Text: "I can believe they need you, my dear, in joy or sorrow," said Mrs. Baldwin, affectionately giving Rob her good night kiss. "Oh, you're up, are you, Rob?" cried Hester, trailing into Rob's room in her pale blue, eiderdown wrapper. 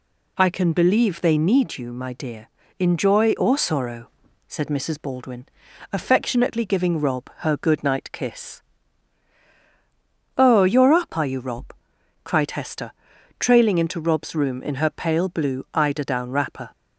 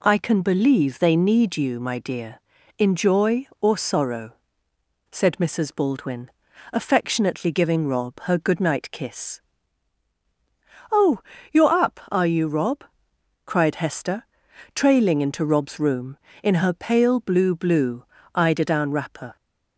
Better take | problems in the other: first | says "blue" twice; at 17.5 s

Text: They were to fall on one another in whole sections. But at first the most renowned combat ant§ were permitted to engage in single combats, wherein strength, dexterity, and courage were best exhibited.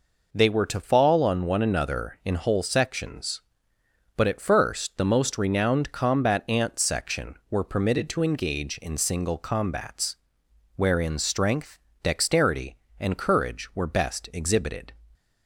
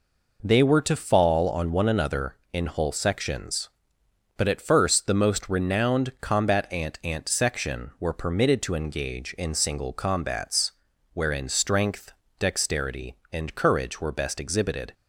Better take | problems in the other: first | says "ant" twice; at 7.0 s

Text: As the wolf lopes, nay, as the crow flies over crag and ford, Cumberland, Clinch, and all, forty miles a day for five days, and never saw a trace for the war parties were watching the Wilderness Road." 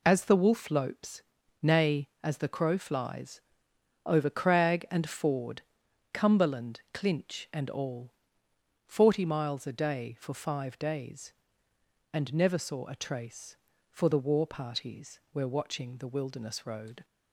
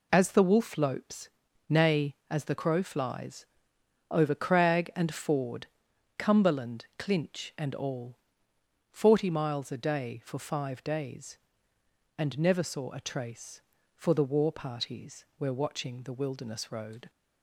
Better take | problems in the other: neither | pauses between "flies" and "over"; noticeable; the same in both

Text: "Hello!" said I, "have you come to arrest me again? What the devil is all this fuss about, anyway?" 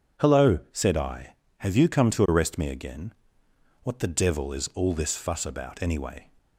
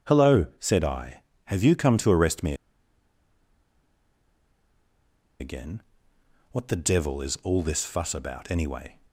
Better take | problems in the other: first | pauses between "me" and "again"; strong; at 2.5 s; 2.8 s long

